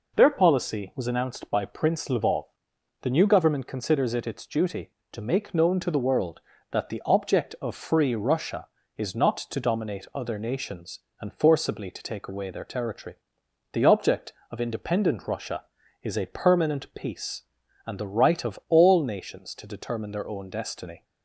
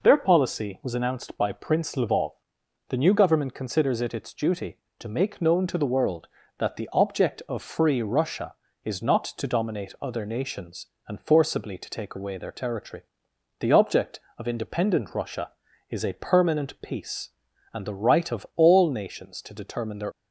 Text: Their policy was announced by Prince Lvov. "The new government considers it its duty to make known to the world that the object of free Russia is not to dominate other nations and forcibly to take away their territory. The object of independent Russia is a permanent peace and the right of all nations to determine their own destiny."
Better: first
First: none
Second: stops before "own destiny"; at 20.1 s

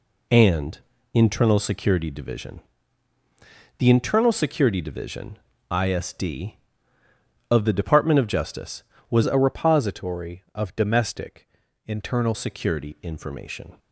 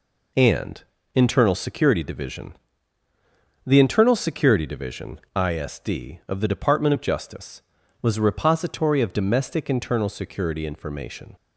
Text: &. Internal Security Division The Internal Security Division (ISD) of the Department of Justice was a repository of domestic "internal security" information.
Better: second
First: pauses between "Division" and "The"; at 2.6 s; 1.1 s long // changes voice from "a" to "internal"; from 9.2 to 12.3 s; 3.1 s long // pauses between "domestic" and "internal"; slight; at 11.4 s; 0.36 s long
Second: pauses between "Division" and "The"; at 2.5 s; 1.1 s long

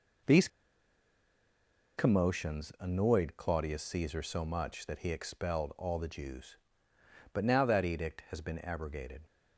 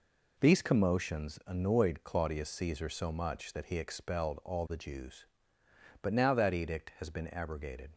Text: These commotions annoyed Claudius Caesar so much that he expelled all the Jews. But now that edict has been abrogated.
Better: second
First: pauses between "These" and "commotions"; strong; at 0.4 s; 1.5 s long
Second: none

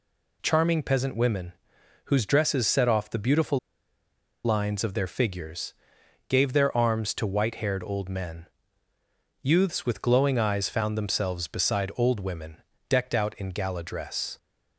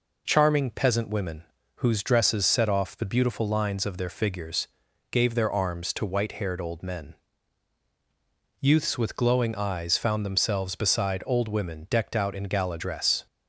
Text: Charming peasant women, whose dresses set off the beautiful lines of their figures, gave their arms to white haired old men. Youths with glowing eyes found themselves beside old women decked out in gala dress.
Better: second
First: pauses between "beautiful" and "lines"; noticeable; at 3.5 s; 0.86 s long // pauses between "women" and "decked"; slight; at 12.5 s; 0.30 s long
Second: none

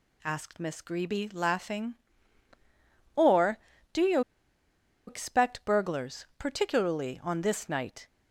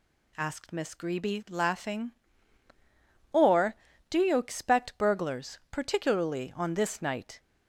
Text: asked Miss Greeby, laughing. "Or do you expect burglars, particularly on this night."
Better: second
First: pauses between "you" and "expect"; noticeable; at 4.2 s; 0.87 s long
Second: none

